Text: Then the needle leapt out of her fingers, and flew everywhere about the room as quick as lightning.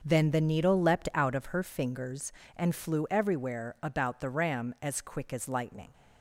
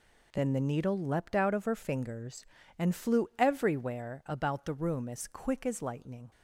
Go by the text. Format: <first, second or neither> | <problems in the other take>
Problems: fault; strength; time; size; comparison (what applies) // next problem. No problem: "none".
second | starts louder than the rest; until 1.0 s; 6 dB // says "ram" for "room"; at 4.2 s